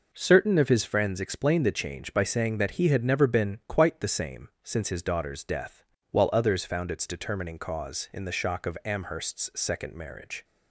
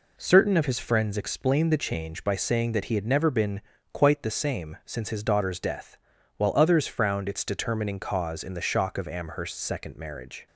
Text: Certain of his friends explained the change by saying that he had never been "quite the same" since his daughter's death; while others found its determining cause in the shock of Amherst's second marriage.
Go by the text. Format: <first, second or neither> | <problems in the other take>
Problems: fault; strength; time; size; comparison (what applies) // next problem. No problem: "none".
first | pauses between "been" and "quite"; slight; at 3.6 s; 0.32 s long // says "frowned" for "found"; at 6.8 s